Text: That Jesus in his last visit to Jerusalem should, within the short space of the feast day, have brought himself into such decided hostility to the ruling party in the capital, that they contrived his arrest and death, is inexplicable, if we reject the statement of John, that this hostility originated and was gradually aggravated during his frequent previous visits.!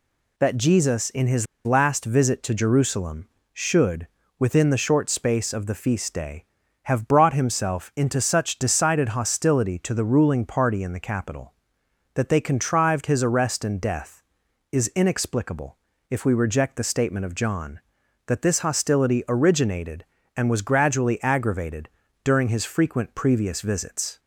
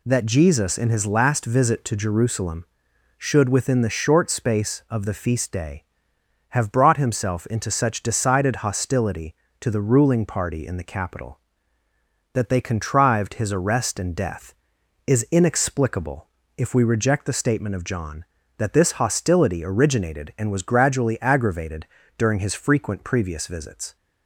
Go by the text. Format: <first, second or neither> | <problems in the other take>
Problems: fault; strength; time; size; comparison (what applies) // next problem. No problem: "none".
second | pauses between "his" and "last"; slight; at 1.4 s; 0.19 s long // pauses between "aggravated" and "during"; slight; at 21.8 s; 0.34 s long; slight in the second